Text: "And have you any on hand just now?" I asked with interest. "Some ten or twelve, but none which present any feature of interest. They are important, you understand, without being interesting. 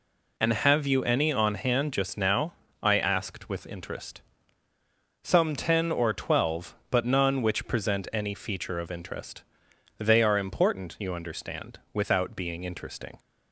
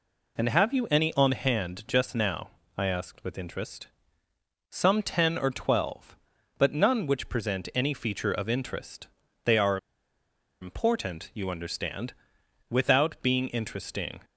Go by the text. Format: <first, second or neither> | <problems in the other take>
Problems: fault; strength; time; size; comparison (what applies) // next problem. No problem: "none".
first | pauses between "are" and "important"; noticeable; at 9.7 s; 0.82 s long